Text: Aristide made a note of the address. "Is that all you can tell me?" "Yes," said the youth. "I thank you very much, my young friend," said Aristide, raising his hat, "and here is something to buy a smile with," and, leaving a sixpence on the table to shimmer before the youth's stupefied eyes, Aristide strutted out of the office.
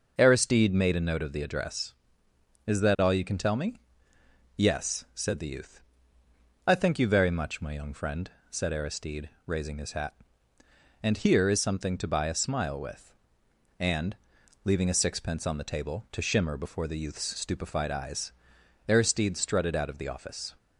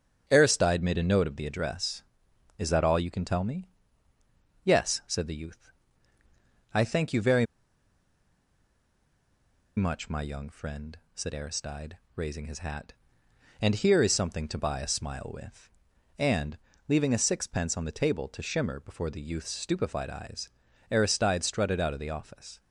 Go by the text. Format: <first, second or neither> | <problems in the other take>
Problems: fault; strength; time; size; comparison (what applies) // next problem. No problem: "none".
first | starts louder than the rest; until 1.2 s; 7 dB // pauses between "very" and "much"; strong; at 7.4 s; 2.3 s long